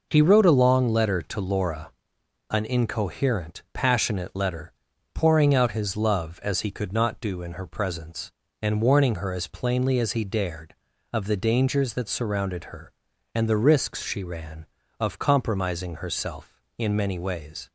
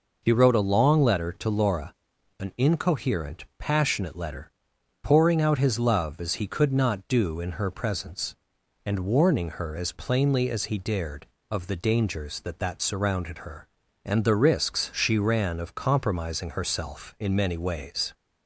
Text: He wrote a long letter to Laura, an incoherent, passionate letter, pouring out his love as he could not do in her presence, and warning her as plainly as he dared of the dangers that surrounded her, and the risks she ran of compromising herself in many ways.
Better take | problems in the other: first | says "that" twice; at 12.5 s

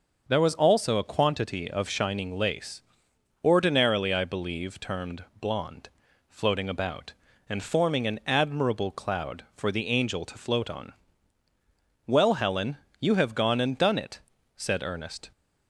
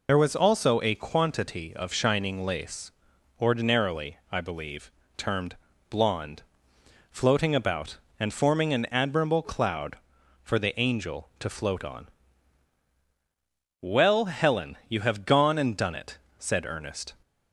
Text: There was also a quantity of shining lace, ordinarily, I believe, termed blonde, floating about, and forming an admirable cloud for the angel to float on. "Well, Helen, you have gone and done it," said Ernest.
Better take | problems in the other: first | loses the start of "There"; at 0.0 s; 85 ms // pauses between "termed" and "blonde"; slight; at 5.5 s; 0.36 s long; slight in the first

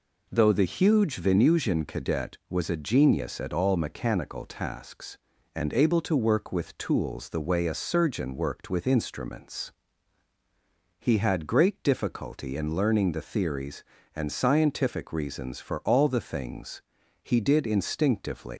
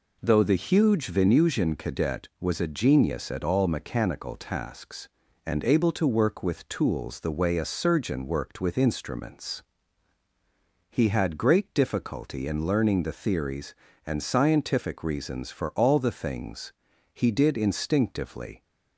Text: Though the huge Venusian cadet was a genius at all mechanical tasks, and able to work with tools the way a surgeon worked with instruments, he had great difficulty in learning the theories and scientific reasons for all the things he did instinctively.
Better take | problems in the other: second | pauses between "things" and "he"; at 16.8 s; 0.40 s long; also in the second // leaves "instinctively" unfinished; at 18.5 s; 140 ms

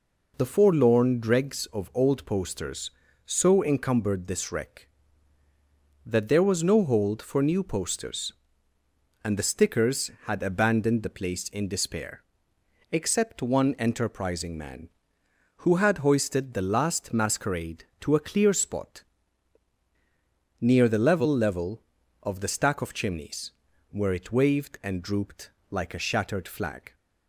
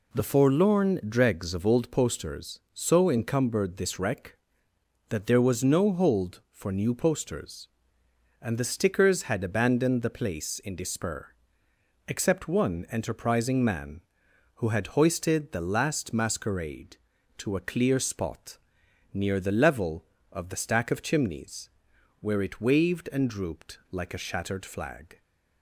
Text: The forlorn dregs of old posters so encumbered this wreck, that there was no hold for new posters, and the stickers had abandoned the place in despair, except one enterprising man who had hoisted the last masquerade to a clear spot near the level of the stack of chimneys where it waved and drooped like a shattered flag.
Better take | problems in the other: second | pauses between "spot" and "near"; strong; at 19.0 s; 1.5 s long; noticeable in the second // says "level" twice; at 21.3 s // pauses between "chimneys" and "where"; at 23.5 s; 0.40 s long; noticeable in the second // pauses between "drooped" and "like"; slight; at 25.4 s; 0.20 s long

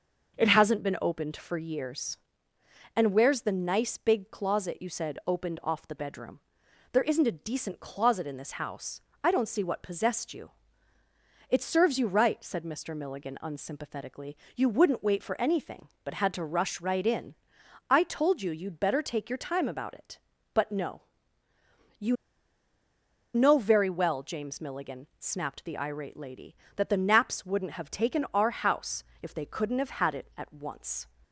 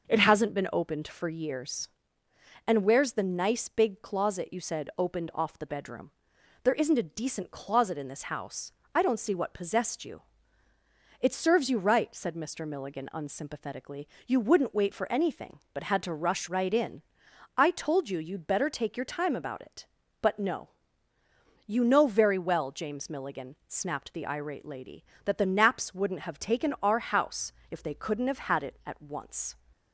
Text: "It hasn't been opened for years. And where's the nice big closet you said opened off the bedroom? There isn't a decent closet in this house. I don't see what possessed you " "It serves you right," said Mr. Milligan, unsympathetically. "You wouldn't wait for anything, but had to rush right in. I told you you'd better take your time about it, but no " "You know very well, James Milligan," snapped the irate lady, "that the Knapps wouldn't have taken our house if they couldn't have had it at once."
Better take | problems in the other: second | starts louder than the rest; until 1.3 s; 6 dB; also in the second // pauses between "You" and "know"; at 22.1 s; 1.1 s long // pauses between "house" and "if"; slight; at 29.0 s; 0.18 s long; slight in the second

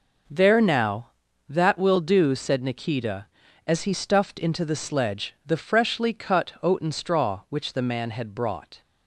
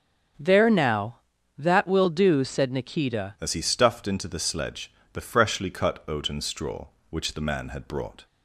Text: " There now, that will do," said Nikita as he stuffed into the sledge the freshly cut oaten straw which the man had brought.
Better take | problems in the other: first | changes voice at "as"; from 3.3 s on; 4.9 s long // pauses between "sledge" and "the"; slight; at 4.9 s; 0.22 s long

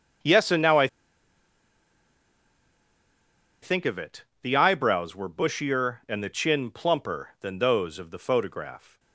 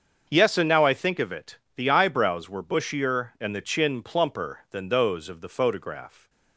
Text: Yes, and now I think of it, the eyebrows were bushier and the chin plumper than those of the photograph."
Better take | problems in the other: second | starts louder than the rest; until 3.9 s; 7 dB; also in the second // pauses between "I" and "think"; strong; at 0.8 s; 2.7 s long

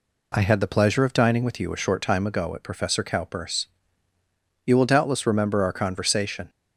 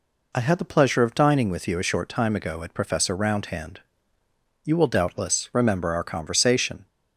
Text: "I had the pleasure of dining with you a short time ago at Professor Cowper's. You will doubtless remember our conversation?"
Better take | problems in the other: first | says "Roundhand" for "Cowper's"; at 3.1 s

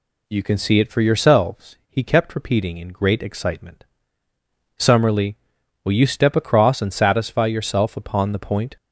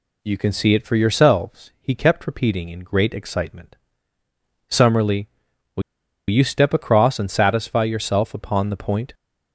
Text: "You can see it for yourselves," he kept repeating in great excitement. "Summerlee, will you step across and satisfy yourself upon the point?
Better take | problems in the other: first | pauses between "will" and "you"; noticeable; at 5.8 s; 0.48 s long

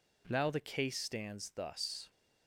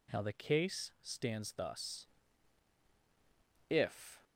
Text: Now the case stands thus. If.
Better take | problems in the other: second | stops before "If"; at 2.0 s

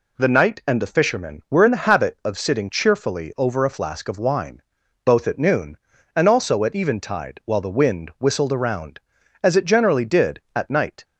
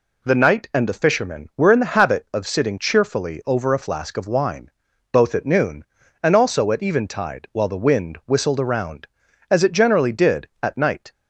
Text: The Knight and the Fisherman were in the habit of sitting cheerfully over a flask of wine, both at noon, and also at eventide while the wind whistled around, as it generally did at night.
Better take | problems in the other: neither | none

